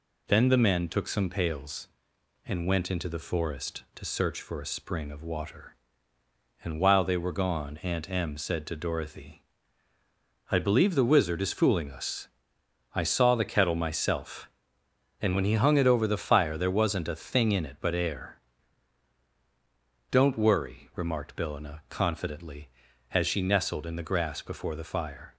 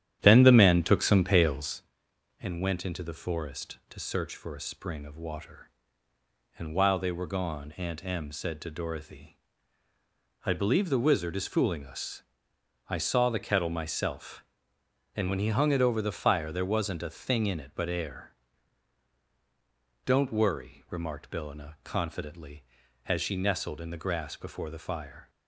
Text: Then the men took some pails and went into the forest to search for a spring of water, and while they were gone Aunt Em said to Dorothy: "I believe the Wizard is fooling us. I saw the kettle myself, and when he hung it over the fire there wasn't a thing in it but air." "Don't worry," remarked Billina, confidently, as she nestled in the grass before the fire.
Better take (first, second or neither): first